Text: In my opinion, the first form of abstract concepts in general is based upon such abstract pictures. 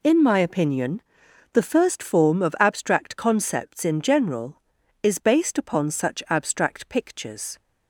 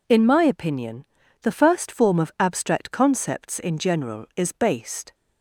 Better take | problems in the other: first | stops before "upon such abstract pictures"; at 5.1 s

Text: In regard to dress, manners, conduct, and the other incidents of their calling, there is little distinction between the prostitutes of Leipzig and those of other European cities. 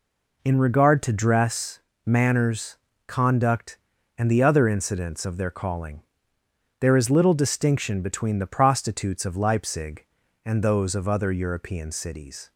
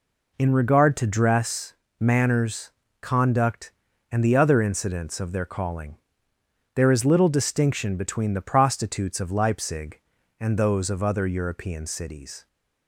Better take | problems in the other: neither | none

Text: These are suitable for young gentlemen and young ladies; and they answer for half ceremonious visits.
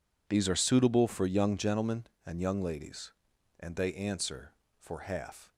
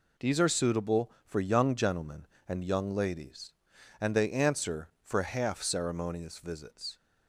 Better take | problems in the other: second | stops before "ceremonious visits"; at 5.5 s

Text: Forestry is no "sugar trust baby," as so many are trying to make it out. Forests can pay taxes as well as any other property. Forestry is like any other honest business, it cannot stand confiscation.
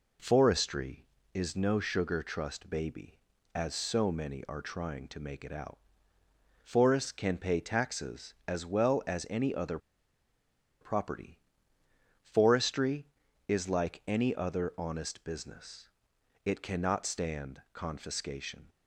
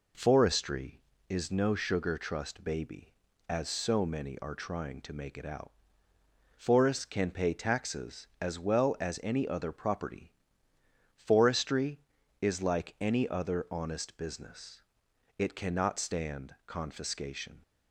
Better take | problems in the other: second | pauses between "other" and "property"; at 9.7 s; 1.0 s long

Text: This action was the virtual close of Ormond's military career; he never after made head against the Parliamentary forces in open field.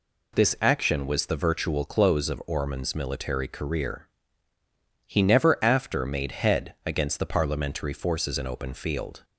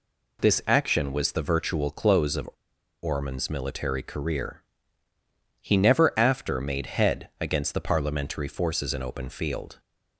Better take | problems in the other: first | pauses between "of" and "Ormond's"; noticeable; at 2.4 s; 0.54 s long

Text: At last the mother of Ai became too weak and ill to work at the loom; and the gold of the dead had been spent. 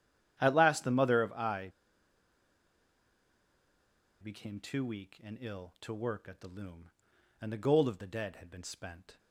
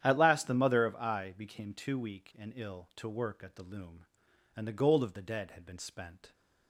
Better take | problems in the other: second | starts louder than the rest; strong; until 1.4 s; 10 dB; strong in the second // pauses between "Ai" and "became"; strong; at 1.7 s; 2.5 s long

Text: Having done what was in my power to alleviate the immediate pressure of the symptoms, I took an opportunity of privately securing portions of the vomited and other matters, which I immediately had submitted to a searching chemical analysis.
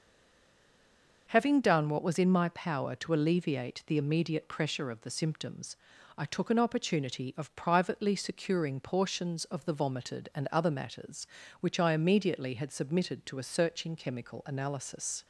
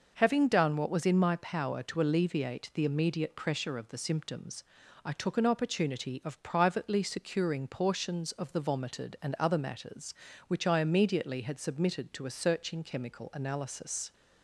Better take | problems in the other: second | stays silent before the first word; noticeable; until 1.2 s; 1.2 s long

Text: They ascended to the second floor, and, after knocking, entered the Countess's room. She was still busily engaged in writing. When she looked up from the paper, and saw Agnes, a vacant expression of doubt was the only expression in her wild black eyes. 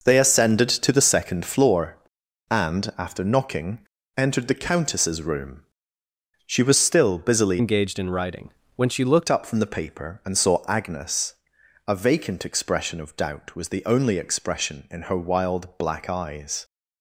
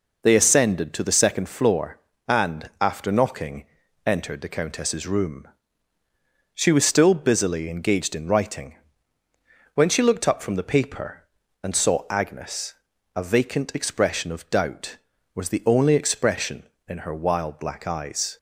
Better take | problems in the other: second | changes voice from "engaged" to "looked"; from 7.5 to 9.2 s; 1.7 s long

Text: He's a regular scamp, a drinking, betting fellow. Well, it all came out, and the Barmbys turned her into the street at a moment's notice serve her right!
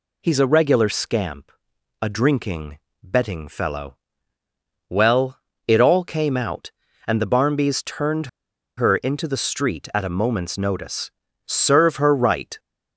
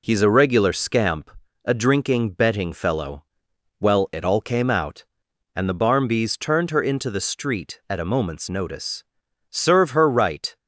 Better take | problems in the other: second | pauses between "turned" and "her"; noticeable; at 8.2 s; 0.50 s long // pauses between "notice" and "serve"; slight; at 11.1 s; 0.36 s long; also in the second

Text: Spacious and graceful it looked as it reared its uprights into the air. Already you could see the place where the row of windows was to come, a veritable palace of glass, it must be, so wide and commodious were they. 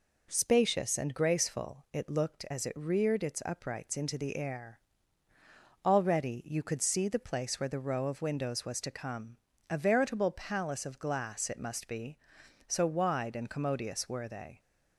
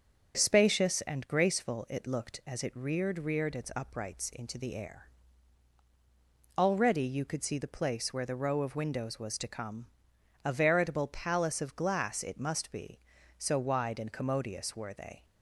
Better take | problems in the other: first | starts louder than the rest; until 1.4 s; 7 dB // says "reared" twice; at 3.1 s

